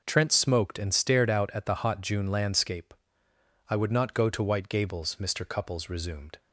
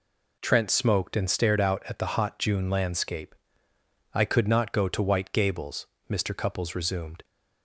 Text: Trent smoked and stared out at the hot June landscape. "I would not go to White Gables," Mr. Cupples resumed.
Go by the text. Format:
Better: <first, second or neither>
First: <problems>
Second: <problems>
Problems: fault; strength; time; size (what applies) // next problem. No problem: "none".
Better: first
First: none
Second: says "could" for "would"; at 4.2 s